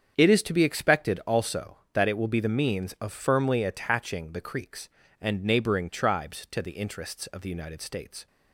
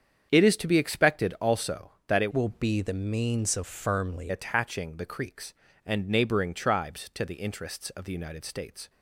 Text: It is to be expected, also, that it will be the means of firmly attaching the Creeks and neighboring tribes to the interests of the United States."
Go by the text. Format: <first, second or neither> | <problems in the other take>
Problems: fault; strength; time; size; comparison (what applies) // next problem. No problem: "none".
first | starts louder than the rest; strong; until 1.3 s; 8 dB; strong in the first // changes voice from "will" to "firmly"; from 2.3 to 4.3 s; 2.0 s long